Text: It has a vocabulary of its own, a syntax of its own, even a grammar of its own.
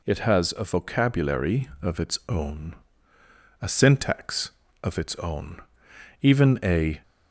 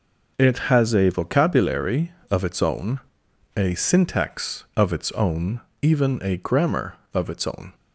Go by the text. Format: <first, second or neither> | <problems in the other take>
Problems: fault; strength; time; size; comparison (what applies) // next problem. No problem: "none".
second | stops before "grammar of its own"; at 7.0 s